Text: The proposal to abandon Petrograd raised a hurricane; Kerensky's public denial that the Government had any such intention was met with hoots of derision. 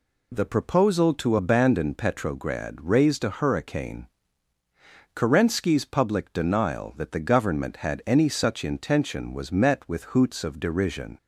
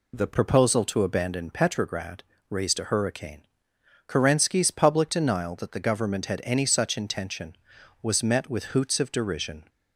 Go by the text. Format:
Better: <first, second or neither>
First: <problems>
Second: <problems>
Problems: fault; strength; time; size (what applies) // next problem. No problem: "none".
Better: first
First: none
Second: changes voice at "proposal"; from 0.3 s on; 9.3 s long // pauses between "Petrograd" and "raised"; slight; at 2.2 s; 0.26 s long